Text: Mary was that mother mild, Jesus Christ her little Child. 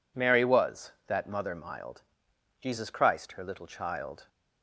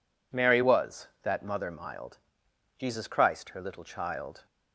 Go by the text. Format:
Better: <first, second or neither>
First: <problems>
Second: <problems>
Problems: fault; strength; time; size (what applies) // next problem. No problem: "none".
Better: neither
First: none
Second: none